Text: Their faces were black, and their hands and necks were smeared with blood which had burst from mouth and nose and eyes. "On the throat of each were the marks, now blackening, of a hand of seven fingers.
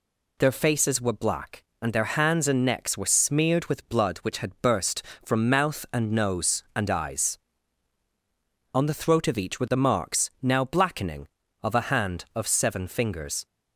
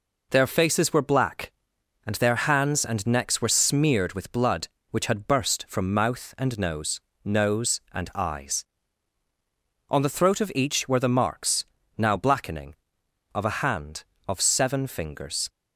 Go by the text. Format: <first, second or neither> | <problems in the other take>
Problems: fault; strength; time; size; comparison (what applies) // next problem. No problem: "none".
first | says "nose" twice; at 7.2 s